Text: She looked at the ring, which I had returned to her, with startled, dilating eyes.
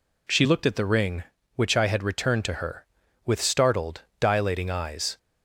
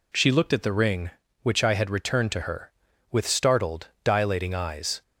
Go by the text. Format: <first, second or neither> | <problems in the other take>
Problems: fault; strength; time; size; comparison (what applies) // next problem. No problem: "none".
neither | none